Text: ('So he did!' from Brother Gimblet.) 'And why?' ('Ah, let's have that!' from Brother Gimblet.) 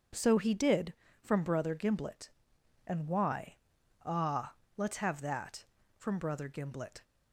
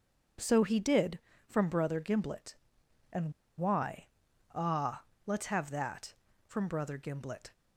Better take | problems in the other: first | pauses between "And" and "why"; slight; at 3.3 s; 0.25 s long

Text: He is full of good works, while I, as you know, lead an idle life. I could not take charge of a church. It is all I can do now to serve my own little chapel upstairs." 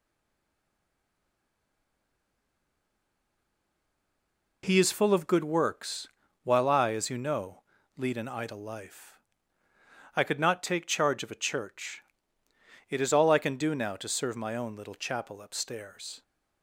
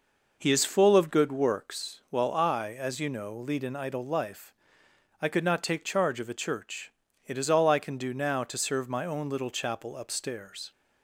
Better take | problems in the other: second | stays silent before the first word; strong; until 4.6 s; 4.6 s long

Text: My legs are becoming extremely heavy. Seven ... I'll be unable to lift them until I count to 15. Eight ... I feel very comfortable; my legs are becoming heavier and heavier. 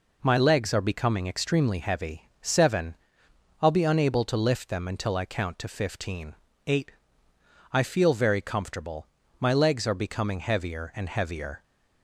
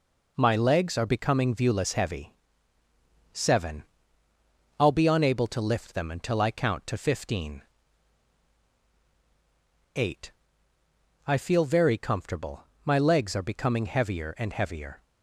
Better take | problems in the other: first | says "viewless" for "extremely"; at 1.5 s

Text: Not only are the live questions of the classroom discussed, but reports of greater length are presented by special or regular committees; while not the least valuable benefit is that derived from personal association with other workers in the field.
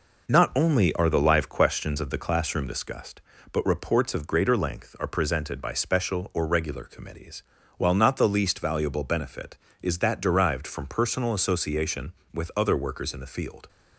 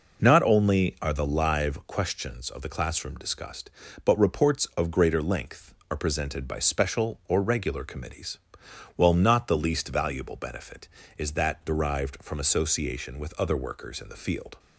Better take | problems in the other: first | skips "personal"; at 12.3 s

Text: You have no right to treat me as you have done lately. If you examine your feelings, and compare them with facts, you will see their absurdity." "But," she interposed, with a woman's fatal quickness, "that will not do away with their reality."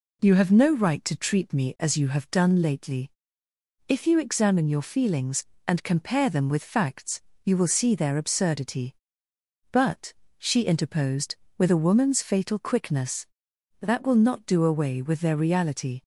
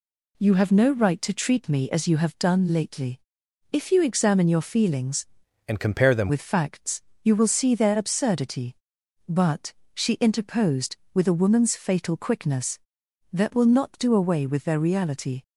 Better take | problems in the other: first | changes voice from "and" to "them"; from 5.6 to 6.2 s; 0.6 s long

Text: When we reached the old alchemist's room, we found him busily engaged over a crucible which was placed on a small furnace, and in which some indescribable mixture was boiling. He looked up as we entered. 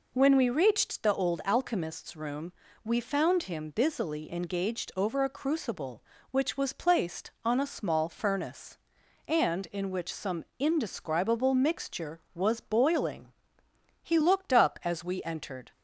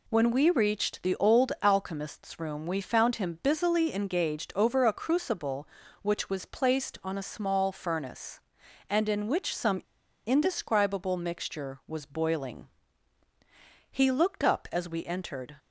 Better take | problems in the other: first | pauses between "some" and "indescribable"; at 9.8 s; 0.43 s long

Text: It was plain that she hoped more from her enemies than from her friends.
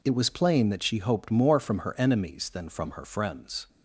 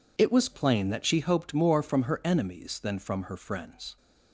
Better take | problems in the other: neither | none

